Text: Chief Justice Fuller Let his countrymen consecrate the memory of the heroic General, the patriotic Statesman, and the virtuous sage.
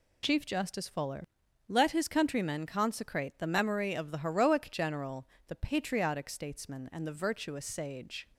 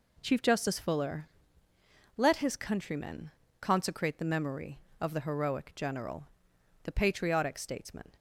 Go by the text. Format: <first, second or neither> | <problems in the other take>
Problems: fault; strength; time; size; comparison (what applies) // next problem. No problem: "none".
first | pauses between "Fuller" and "Let"; noticeable; at 1.2 s; 0.90 s long; also in the first // pauses between "countrymen" and "consecrate"; slight; at 3.2 s; 0.32 s long // stops before "and the virtuous sage"; at 8.1 s